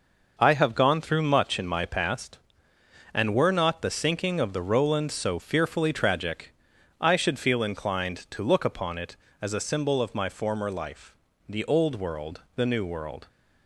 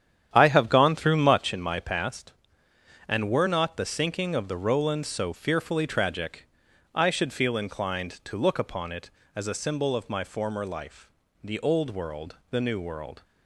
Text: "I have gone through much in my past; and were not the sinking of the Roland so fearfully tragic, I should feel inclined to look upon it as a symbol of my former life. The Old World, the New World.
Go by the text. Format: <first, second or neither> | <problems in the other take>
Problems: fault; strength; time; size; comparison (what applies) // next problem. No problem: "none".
first | starts louder than the rest; strong; until 1.5 s; 9.5 dB